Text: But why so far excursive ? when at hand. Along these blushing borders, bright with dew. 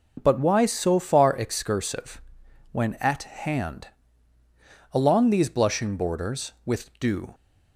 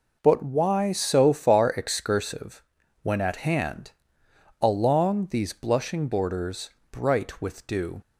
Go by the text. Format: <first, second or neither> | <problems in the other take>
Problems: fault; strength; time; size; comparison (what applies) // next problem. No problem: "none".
second | skips "bright"; at 6.5 s